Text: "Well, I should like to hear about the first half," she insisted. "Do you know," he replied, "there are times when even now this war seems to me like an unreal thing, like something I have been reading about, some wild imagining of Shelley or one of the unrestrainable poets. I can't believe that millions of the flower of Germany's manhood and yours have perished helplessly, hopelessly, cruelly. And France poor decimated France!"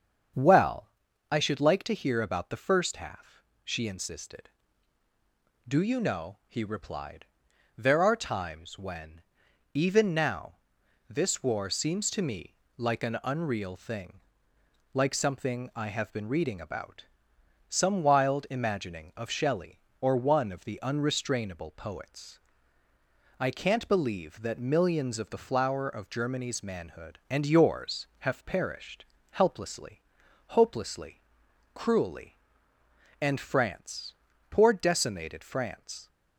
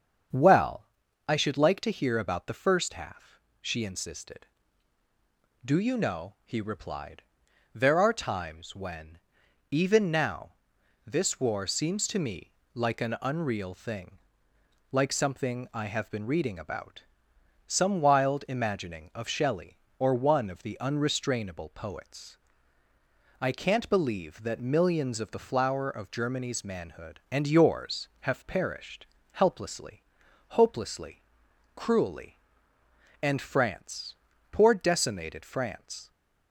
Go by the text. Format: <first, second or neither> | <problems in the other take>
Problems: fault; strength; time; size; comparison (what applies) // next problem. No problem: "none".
neither | starts louder than the rest; strong; the same in both // pauses between "when" and "even"; noticeable; the same in both // pauses between "now" and "this"; noticeable; the same in both // pauses between "me" and "like"; slight; the same in both // pauses between "perished" and "helplessly"; slight; the same in both // pauses between "France" and "poor"; the same in both